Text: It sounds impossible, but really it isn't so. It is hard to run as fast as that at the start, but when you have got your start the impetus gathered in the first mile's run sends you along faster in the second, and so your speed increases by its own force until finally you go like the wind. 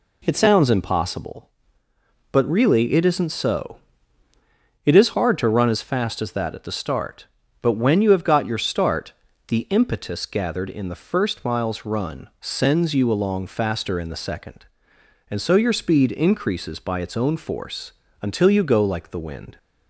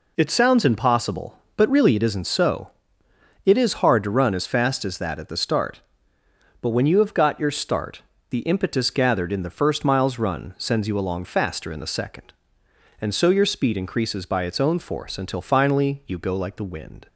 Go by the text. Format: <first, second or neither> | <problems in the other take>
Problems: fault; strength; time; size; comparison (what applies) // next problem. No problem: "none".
second | pauses between "start" and "the"; slight; at 9.1 s; 0.36 s long; slight in the second // pauses between "force" and "until"; slight; at 17.9 s; 0.30 s long // skips "finally"; at 18.4 s